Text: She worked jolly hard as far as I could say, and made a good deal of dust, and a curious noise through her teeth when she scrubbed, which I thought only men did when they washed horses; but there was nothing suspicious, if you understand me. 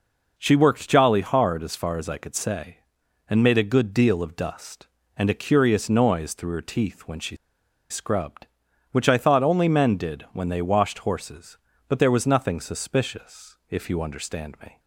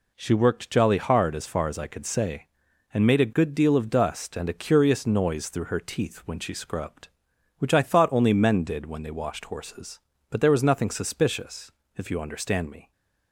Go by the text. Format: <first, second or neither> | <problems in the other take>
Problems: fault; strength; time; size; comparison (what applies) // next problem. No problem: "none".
second | pauses between "she" and "scrubbed"; noticeable; at 7.3 s; 0.54 s long